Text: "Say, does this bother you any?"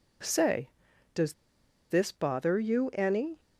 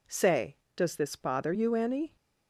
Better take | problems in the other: second | pauses between "does" and "this"; noticeable; at 1.3 s; 0.56 s long

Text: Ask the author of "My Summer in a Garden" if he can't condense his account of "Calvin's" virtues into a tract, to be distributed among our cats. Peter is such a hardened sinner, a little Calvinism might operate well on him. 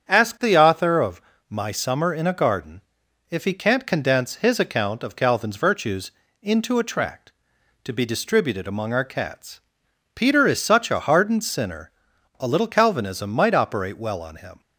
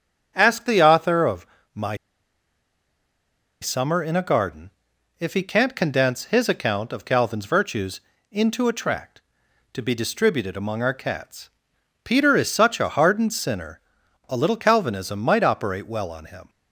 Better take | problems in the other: first | starts louder than the rest; strong; until 1.3 s; 8 dB; strong in the first // pauses between "of" and "My"; slight; at 1.4 s; 0.30 s long; slight in the first // pauses between "My" and "Summer"; strong; at 1.9 s; 1.6 s long // pauses between "Garden" and "if"; noticeable; at 4.6 s; 0.48 s long; noticeable in the first // pauses between "virtues" and "into"; slight; at 8.0 s; 0.28 s long; slight in the first

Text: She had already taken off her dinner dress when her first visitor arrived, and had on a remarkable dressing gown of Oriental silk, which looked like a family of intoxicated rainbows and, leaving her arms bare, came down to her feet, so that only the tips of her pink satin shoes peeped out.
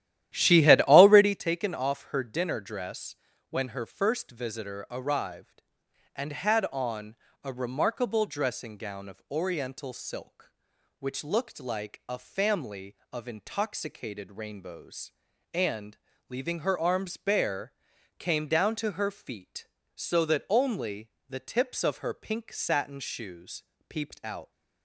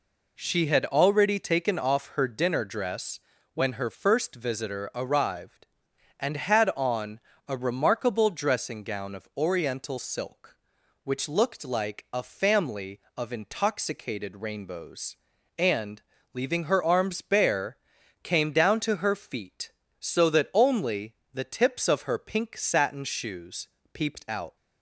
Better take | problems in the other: second | starts louder than the rest; strong; until 1.4 s; 12.5 dB // pauses between "dress" and "when"; slight; at 3.1 s; 0.36 s long; slight in the second // pauses between "on" and "a"; slight; at 7.1 s; 0.28 s long; slight in the second // pauses between "only" and "the"; slight; at 21.0 s; 0.20 s long; slight in the second // pauses between "shoes" and "peeped"; slight; at 23.6 s; 0.24 s long; slight in the second

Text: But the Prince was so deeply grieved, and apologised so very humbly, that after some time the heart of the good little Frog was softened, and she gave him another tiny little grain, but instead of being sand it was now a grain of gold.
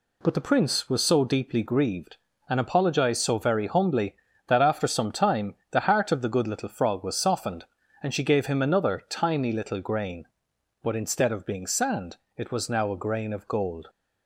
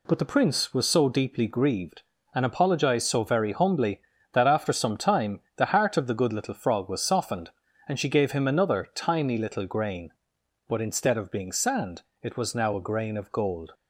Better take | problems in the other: neither | pauses between "time" and "the"; slight; the same in both // pauses between "sand" and "it"; slight; the same in both

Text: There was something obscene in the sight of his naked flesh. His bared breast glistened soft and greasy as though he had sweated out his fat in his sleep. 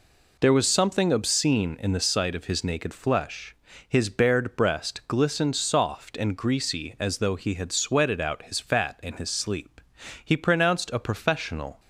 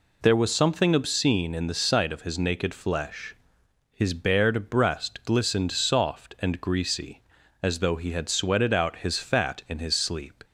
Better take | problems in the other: second | goes on to say "He pronounced a professional"; from 10.2 s on; 1.5 s long

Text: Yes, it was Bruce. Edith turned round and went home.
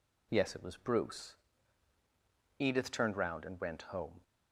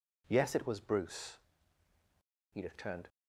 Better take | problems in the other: first | stops before "round and went home"; at 3.0 s

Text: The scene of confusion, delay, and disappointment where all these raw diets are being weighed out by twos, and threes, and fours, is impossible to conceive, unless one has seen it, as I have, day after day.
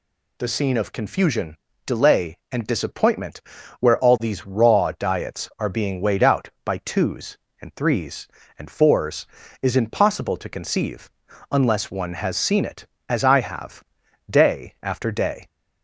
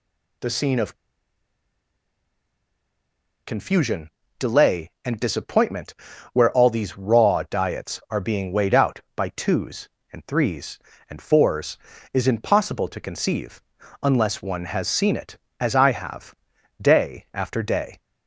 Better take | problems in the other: first | pauses between "of" and "confusion"; strong; at 0.9 s; 2.5 s long // pauses between "disappointment" and "where"; at 5.9 s; 0.40 s long; also in the first

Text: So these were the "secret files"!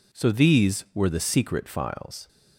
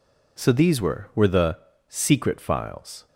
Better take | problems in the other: first | says "were" twice; at 1.1 s // pauses between "the" and "secret"; slight; at 1.5 s; 0.32 s long

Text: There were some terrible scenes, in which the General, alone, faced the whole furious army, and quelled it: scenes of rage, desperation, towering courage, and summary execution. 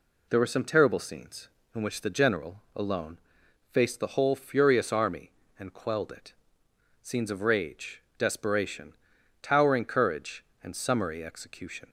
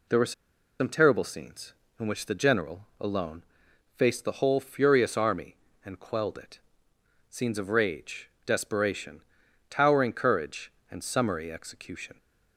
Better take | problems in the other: first | pauses between "were" and "some"; noticeable; at 0.3 s; 0.46 s long

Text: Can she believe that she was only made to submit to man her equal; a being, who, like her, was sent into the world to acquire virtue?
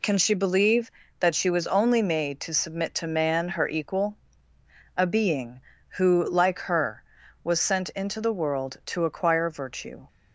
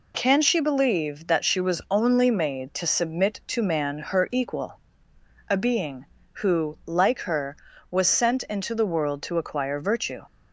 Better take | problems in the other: neither | none

